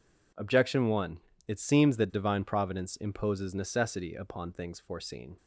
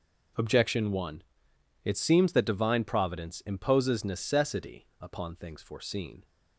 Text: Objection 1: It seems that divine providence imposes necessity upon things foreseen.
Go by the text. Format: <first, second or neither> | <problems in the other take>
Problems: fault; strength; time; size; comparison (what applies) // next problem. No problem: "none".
neither | none